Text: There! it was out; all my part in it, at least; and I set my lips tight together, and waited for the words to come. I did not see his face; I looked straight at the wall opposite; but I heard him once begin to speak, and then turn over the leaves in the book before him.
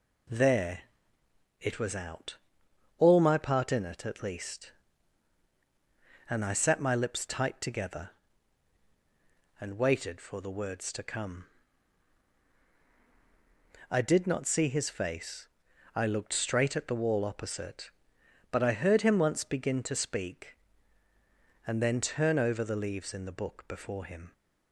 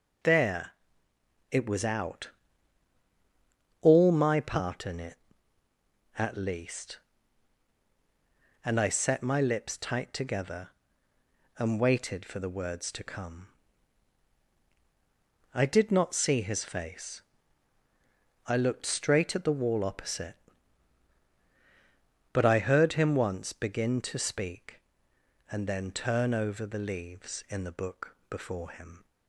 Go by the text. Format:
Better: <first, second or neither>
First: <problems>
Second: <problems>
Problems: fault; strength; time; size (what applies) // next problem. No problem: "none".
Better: neither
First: none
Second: none